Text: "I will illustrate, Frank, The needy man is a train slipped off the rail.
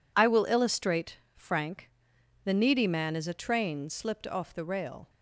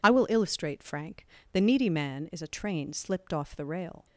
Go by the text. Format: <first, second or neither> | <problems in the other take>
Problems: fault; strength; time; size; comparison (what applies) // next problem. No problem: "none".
neither | none